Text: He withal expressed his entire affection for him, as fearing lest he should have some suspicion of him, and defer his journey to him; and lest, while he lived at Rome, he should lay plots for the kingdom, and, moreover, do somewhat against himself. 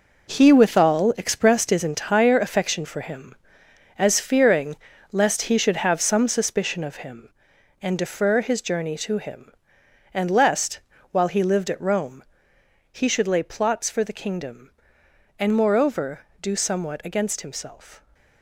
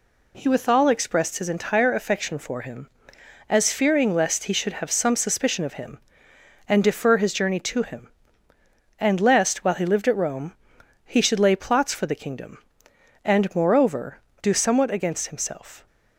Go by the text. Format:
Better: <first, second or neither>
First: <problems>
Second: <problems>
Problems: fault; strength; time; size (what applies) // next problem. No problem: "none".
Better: second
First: gets quieter; strong; throughout; 9.5 dB // pauses between "fearing" and "lest"; slight; at 4.7 s; 0.34 s long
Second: none